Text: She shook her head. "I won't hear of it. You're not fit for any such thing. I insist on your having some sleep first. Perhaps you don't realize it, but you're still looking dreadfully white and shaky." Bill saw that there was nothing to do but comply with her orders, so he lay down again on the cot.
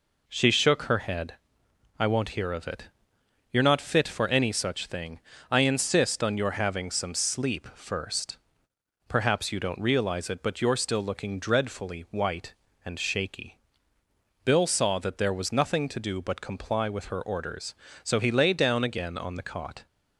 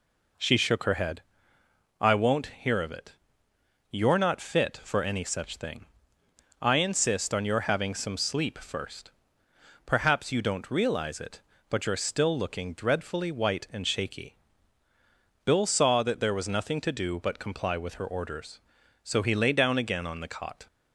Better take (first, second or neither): neither